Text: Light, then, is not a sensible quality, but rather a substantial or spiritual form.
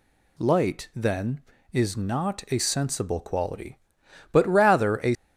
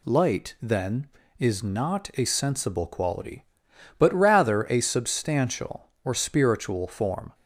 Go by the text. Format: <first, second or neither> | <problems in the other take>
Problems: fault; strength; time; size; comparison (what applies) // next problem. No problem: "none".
second | stops before "substantial or spiritual form"; at 5.1 s